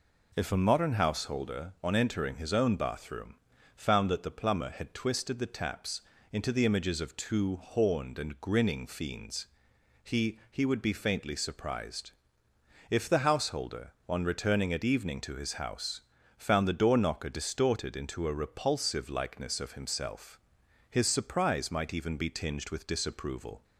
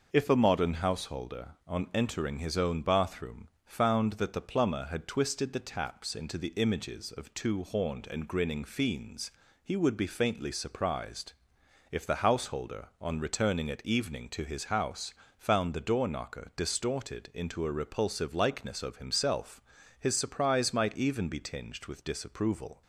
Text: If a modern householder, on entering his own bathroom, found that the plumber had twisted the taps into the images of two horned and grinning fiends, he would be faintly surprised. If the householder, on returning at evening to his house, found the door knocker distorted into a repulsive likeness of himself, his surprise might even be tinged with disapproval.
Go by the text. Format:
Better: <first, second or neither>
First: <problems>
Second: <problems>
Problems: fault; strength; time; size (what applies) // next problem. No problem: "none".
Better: second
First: pauses between "taps" and "into"; slight; at 6.0 s; 0.30 s long // says "he" twice; at 10.5 s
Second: none